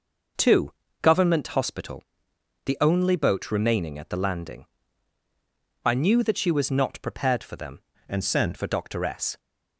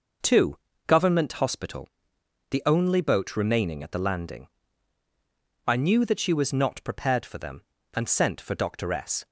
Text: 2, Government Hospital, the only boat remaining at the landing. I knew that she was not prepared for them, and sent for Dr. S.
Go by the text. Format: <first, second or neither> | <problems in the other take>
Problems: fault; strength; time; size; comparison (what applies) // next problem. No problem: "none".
second | changes voice from "and" to "sent"; from 8.0 to 8.5 s; 0.5 s long